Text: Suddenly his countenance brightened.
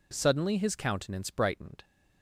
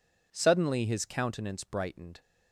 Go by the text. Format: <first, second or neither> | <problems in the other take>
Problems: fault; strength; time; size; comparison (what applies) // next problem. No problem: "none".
neither | none